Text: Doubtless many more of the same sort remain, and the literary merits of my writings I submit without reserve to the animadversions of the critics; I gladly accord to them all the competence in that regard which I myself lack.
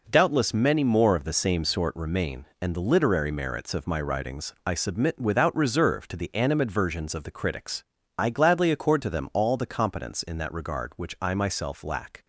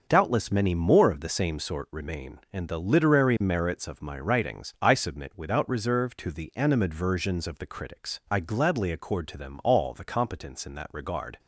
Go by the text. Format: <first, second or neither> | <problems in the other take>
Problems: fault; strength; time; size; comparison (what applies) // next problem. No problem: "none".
first | starts louder than the rest; until 1.0 s; 6.5 dB // stops before "which I myself lack"; at 11.3 s